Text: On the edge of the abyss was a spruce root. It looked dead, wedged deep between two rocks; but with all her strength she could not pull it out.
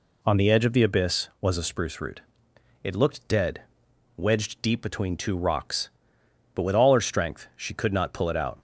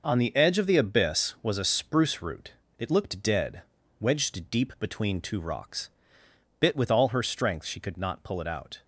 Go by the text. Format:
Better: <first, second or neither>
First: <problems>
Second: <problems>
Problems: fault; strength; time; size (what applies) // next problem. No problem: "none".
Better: first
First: none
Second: says "bit" for "but"; at 6.5 s